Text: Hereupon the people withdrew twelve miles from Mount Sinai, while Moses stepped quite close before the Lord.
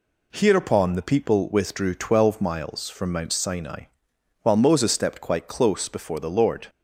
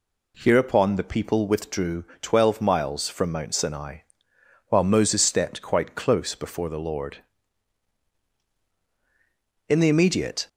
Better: first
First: none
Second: pauses between "withdrew" and "twelve"; slight; at 2.0 s; 0.17 s long // goes on to say "In the immediate"; noticeable; from 9.6 s on; 0.80 s long

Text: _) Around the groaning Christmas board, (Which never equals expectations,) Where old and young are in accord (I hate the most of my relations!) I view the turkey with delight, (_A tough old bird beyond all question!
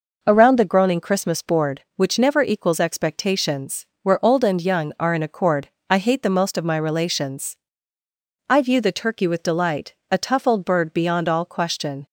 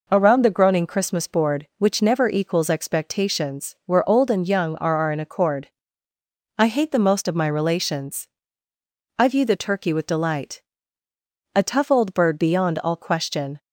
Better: first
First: none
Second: says "are" twice; at 4.9 s

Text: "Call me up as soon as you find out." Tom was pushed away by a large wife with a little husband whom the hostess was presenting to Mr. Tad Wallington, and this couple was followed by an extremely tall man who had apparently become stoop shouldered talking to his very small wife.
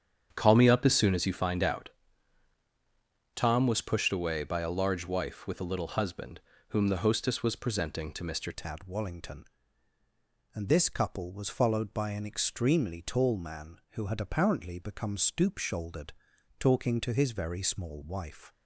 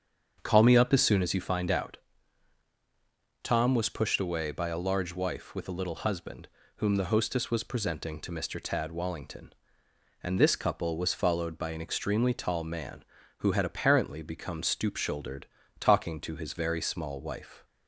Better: second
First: starts louder than the rest; strong; until 1.3 s; 8.5 dB // pauses between "husband" and "whom"; slight; at 6.3 s; 0.30 s long // changes voice at "Tad"; from 8.5 s on; 10.0 s long // pauses between "shouldered" and "talking"; noticeable; at 16.1 s; 0.48 s long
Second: starts louder than the rest; strong; until 1.4 s; 7.5 dB // pauses between "husband" and "whom"; slight; at 6.4 s; 0.30 s long // pauses between "shouldered" and "talking"; slight; at 15.4 s; 0.35 s long

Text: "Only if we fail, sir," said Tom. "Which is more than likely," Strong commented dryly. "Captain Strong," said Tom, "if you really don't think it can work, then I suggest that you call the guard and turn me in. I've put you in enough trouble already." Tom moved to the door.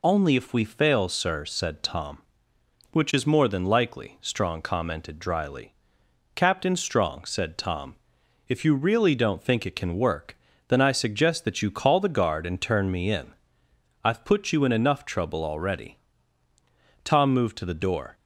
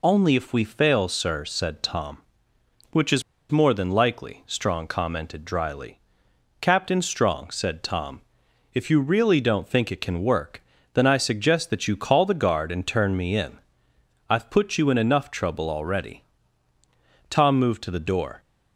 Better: first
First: none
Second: pauses between "is" and "more"; slight; at 3.2 s; 0.29 s long

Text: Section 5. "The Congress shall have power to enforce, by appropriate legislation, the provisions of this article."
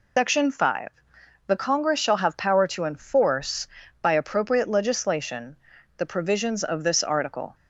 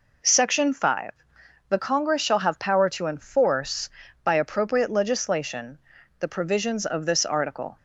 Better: second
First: loses the start of "Section"; at 0.1 s; 150 ms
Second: none

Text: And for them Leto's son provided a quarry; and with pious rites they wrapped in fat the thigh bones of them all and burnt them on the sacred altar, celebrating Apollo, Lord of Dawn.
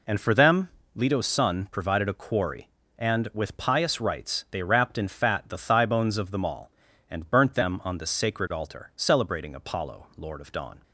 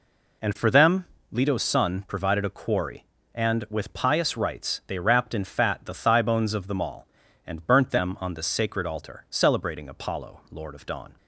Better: neither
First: pauses between "them" and "Leto's"; slight; at 0.6 s; 0.26 s long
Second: pauses between "them" and "Leto's"; slight; at 1.0 s; 0.26 s long

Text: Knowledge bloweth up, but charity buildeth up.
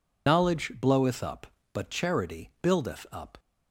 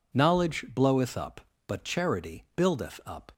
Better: second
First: loses the start of "Knowledge"; at 0.2 s; 55 ms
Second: none

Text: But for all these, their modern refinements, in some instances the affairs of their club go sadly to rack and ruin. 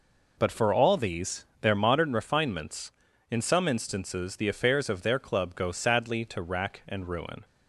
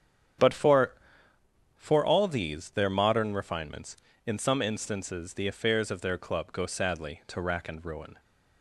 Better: first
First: none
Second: starts louder than the rest; strong; until 2.2 s; 9 dB // says "for" twice; at 1.7 s

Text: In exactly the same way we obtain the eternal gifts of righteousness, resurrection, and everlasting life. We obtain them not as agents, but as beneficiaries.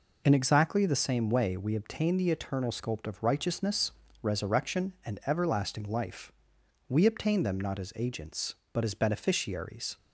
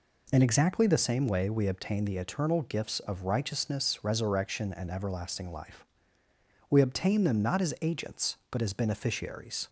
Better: second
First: says "sculpt" for "gifts"; at 2.7 s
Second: none

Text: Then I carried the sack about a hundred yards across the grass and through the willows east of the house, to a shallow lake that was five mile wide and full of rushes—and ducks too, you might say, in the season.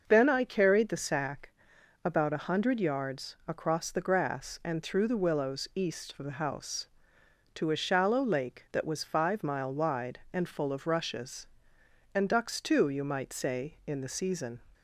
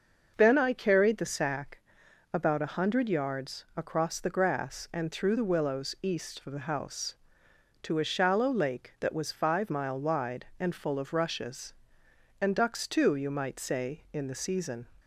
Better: neither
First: starts louder than the rest; until 1.0 s; 6 dB // pauses between "sack" and "about"; noticeable; at 1.5 s; 0.52 s long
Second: starts louder than the rest; until 1.3 s; 6 dB // pauses between "sack" and "about"; noticeable; at 1.7 s; 0.52 s long

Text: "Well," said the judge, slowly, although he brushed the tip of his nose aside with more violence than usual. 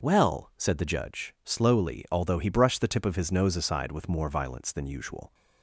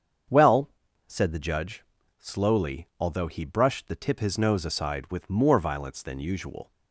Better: first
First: none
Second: starts louder than the rest; strong; until 1.6 s; 7.5 dB // skips "of"; at 4.1 s

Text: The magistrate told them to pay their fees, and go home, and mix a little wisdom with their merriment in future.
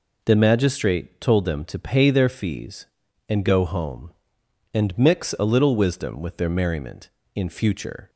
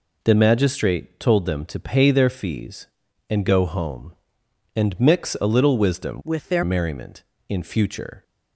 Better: first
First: none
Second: changes voice from "with" to "their"; from 6.2 to 6.6 s; 0.4 s long

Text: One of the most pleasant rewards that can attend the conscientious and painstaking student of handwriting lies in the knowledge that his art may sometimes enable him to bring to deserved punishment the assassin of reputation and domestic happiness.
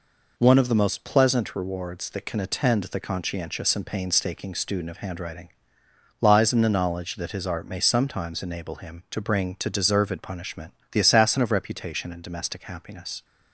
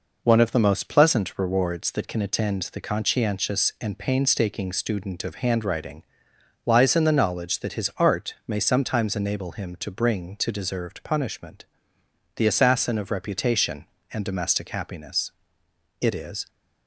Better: first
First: pauses between "handwriting" and "lies"; noticeable; at 5.5 s; 0.70 s long // pauses between "punishment" and "the"; slight; at 10.7 s; 0.18 s long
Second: pauses between "handwriting" and "lies"; noticeable; at 6.0 s; 0.62 s long // pauses between "punishment" and "the"; noticeable; at 11.6 s; 0.70 s long // goes on to say "It is"; slight; from 16.0 s on; 0.48 s long

